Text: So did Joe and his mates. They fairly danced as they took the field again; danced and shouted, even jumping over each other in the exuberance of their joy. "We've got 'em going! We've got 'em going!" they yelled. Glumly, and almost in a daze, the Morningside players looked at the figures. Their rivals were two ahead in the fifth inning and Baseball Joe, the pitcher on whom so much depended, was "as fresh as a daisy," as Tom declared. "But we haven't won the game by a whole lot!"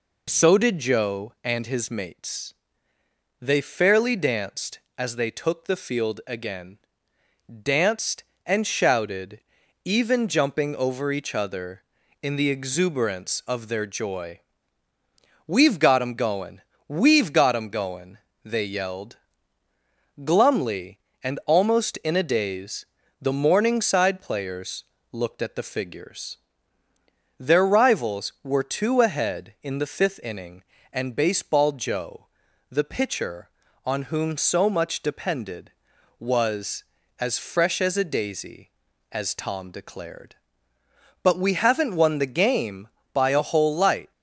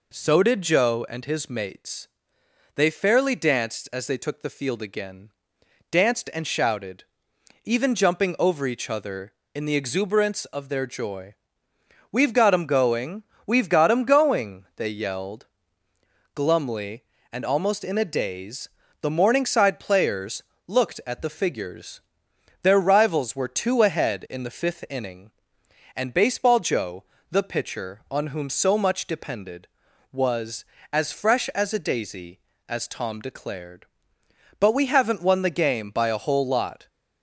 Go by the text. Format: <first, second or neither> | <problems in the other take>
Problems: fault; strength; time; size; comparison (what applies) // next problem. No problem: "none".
second | pauses between "players" and "looked"; slight; at 24.8 s; 0.26 s long; slight in the second // says "light" for "lot"; at 43.7 s